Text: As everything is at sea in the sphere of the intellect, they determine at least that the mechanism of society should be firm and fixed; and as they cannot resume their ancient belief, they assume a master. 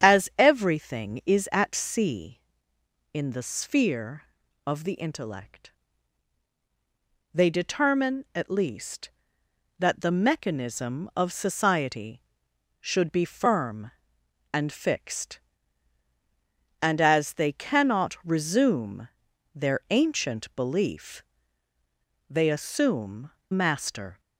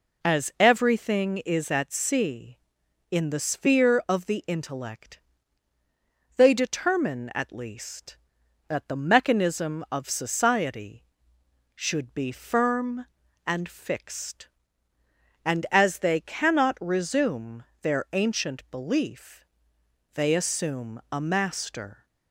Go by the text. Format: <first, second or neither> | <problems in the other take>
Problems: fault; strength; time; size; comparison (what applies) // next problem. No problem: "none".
second | starts louder than the rest; strong; until 1.1 s; 8.5 dB // pauses between "resume" and "their"; noticeable; at 19.0 s; 0.48 s long; slight in the second // skips "a"; at 23.4 s